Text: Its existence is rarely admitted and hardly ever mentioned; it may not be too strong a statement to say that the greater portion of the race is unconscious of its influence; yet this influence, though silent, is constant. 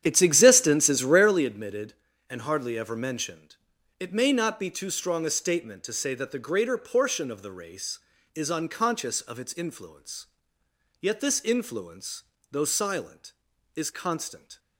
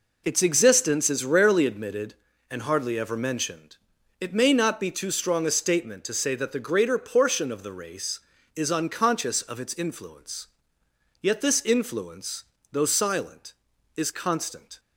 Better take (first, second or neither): second